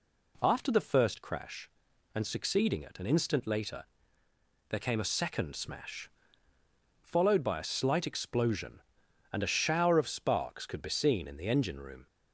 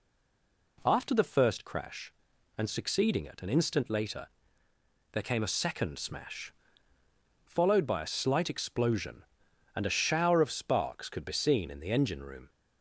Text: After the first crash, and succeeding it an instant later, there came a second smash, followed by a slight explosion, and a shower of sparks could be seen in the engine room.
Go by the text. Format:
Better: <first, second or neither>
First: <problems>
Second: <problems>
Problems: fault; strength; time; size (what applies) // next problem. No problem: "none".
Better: first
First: none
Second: stays silent before the first word; slight; until 0.7 s; 0.7 s long